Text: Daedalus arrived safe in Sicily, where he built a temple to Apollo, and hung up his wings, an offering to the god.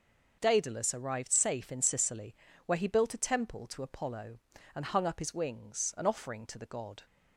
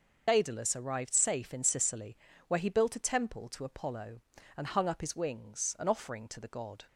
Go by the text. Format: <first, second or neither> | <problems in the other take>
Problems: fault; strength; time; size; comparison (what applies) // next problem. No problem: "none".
first | loses the start of "Daedalus"; at 0.2 s; 55 ms